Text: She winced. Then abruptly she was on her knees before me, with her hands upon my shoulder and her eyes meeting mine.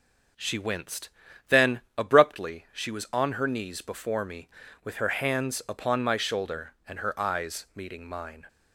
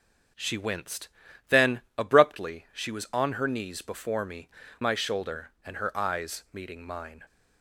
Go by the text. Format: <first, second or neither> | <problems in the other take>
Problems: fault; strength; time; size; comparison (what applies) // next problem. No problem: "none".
first | starts louder than the rest; until 1.7 s; 6.5 dB // pauses between "Then" and "abruptly"; slight; at 1.8 s; 0.16 s long; slight in the first // skips "with her hands upon"; at 4.6 s